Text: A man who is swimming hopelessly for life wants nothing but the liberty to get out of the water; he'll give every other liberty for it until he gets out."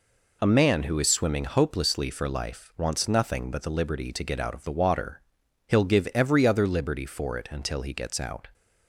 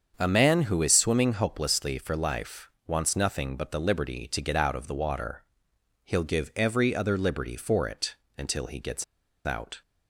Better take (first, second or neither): first